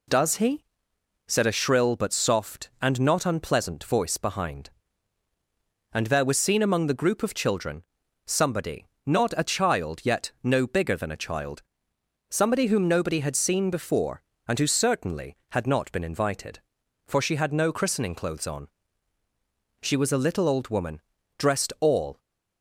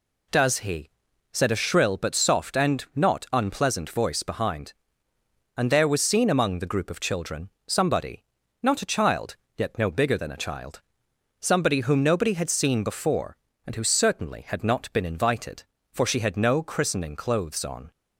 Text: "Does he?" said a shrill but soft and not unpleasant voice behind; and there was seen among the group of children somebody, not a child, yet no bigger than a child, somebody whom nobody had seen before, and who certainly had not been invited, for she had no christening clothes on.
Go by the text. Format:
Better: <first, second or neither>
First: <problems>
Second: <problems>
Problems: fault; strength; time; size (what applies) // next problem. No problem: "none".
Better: second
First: pauses between "children" and "somebody"; at 7.8 s; 0.42 s long // goes on to say "She was a little old woman dressed all"; strong; from 19.8 s on; 2.3 s long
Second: pauses between "children" and "somebody"; slight; at 7.4 s; 0.18 s long